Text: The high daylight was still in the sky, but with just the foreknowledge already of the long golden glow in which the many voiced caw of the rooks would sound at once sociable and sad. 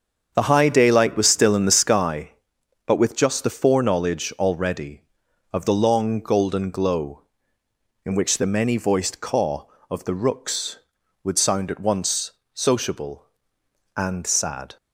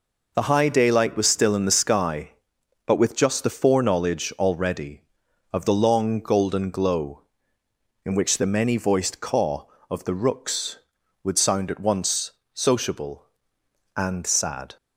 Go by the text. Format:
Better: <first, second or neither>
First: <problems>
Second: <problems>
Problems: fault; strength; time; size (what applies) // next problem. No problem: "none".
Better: second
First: starts louder than the rest; strong; until 2.2 s; 7.5 dB // pauses between "once" and "sociable"; slight; at 12.3 s; 0.24 s long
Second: pauses between "once" and "sociable"; slight; at 12.3 s; 0.24 s long